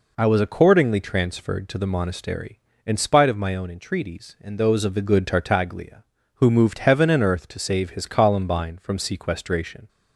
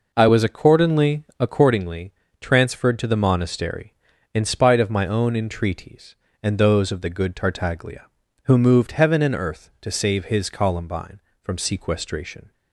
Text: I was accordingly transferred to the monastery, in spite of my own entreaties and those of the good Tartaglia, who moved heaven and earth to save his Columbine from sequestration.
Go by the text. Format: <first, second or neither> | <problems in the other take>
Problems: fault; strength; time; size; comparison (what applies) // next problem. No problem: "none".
first | says "accordingly" twice; at 1.3 s